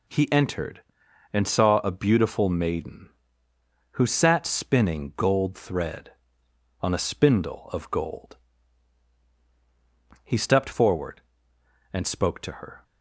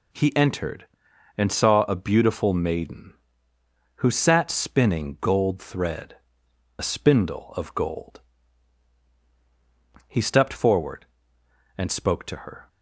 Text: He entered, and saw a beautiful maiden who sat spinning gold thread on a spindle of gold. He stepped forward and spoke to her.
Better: first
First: none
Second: skips "on"; at 6.4 s

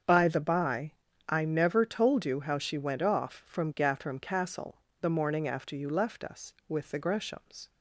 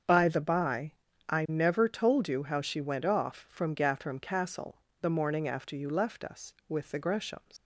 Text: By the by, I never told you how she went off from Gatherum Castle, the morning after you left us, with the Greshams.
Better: first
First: starts louder than the rest; strong; until 1.4 s; 7 dB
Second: starts louder than the rest; until 1.4 s; 7 dB // leaves "Greshams" unfinished; at 7.5 s; 130 ms

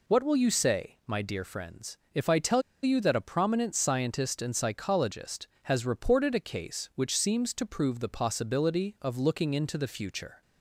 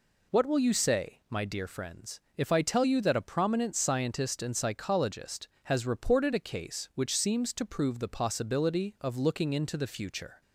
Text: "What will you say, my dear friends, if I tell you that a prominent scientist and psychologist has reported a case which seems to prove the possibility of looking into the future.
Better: second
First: pauses between "tell" and "you"; slight; at 2.6 s; 0.21 s long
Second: none

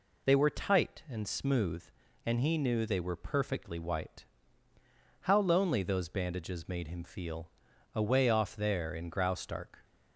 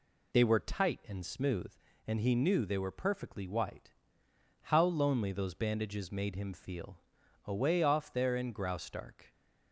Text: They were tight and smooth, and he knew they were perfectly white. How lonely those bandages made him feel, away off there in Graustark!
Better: neither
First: none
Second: none

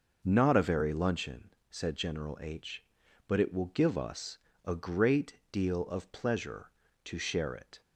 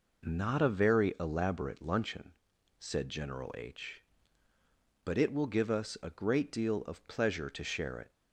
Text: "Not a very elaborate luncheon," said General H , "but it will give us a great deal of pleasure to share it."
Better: second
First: skips "elaborate"; at 0.9 s // pauses between "us" and "a"; slight; at 4.3 s; 0.26 s long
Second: none

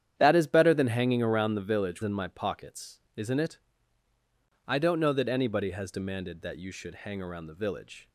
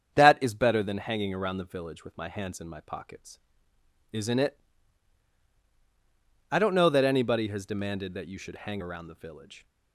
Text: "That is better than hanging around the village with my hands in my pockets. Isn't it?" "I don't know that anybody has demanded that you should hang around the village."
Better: second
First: starts louder than the rest; strong; until 1.1 s; 9.5 dB // skips "with my hands"; at 2.0 s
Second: starts louder than the rest; strong; until 1.2 s; 8 dB

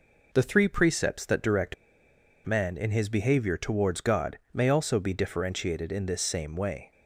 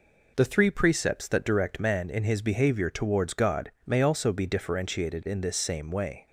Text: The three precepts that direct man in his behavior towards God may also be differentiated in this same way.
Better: second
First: pauses between "direct" and "man"; noticeable; at 1.7 s; 0.69 s long // pauses between "God" and "may"; slight; at 4.3 s; 0.16 s long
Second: pauses between "God" and "may"; slight; at 3.6 s; 0.16 s long

